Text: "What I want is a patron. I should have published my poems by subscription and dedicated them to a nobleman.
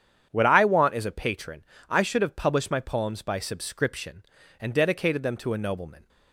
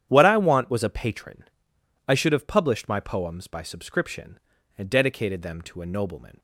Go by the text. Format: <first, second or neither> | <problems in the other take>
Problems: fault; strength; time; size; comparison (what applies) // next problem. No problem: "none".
first | starts louder than the rest; strong; until 1.1 s; 10 dB; strong in the first // says "was" for "is"; at 0.7 s